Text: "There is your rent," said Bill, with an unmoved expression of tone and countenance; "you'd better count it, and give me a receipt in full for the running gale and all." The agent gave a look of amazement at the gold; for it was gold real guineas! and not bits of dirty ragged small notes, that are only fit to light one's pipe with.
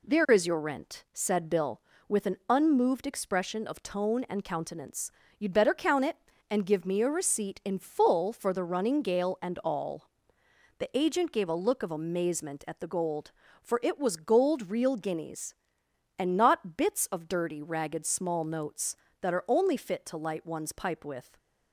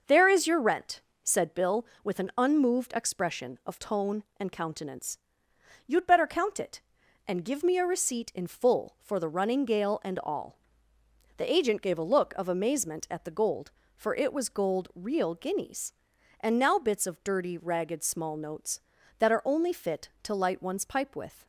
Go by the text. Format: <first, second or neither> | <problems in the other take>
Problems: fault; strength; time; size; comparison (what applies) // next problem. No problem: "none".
first | starts louder than the rest; noticeable; until 1.2 s; 6 dB // says "now" for "not"; at 16.5 s